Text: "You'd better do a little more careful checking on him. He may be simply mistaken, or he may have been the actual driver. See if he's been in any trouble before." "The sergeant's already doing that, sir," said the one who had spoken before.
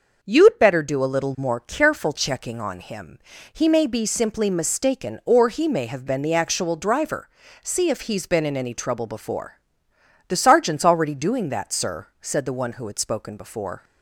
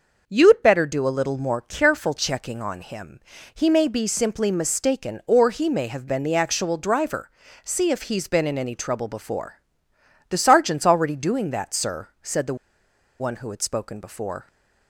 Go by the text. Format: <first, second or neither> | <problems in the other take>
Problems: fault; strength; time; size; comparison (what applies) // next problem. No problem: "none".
first | pauses between "the" and "one"; noticeable; at 12.5 s; 0.62 s long